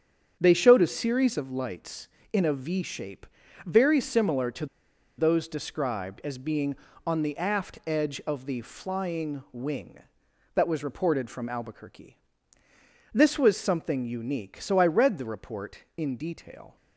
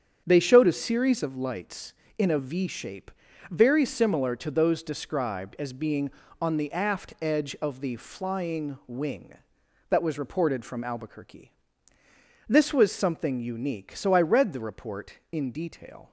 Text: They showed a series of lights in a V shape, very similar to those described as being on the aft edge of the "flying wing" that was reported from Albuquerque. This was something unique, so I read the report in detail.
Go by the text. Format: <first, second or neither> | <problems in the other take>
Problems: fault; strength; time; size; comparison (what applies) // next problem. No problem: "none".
second | starts louder than the rest; strong; until 1.4 s; 7.5 dB; strong in the second // pauses between "to" and "those"; noticeable; at 4.6 s; 0.52 s long